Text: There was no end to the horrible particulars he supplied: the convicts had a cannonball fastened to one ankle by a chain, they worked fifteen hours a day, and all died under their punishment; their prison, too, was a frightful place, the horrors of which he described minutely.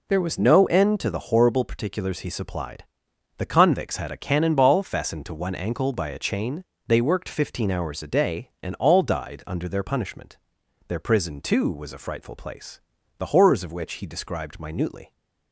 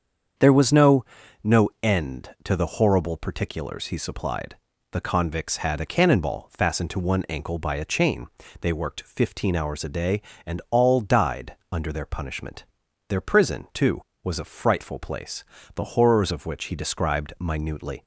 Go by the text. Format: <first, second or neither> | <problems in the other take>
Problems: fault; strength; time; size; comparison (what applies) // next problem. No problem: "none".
first | starts louder than the rest; strong; until 1.9 s; 7.5 dB // says "no" twice; at 1.4 s // pauses between "died" and "under"; slight; at 11.5 s; 0.16 s long